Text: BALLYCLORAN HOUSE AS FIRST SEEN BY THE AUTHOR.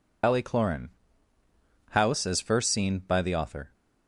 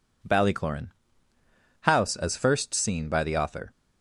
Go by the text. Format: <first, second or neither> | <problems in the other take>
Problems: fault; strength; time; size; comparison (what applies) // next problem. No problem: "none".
second | loses the start of "BALLYCLORAN"; at 0.2 s; 85 ms // pauses between "BALLYCLORAN" and "HOUSE"; noticeable; at 0.9 s; 0.98 s long; noticeable in the second